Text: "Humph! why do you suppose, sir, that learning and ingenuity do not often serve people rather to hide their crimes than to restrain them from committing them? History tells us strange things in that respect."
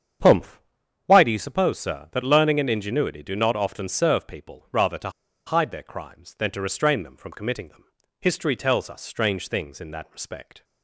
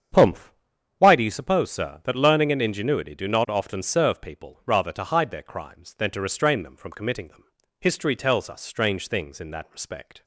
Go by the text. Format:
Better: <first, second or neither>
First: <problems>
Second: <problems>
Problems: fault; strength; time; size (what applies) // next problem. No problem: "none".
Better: second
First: starts louder than the rest; strong; until 1.7 s; 8 dB // pauses between "to" and "hide"; at 5.0 s; 0.37 s long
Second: starts louder than the rest; strong; until 1.6 s; 8 dB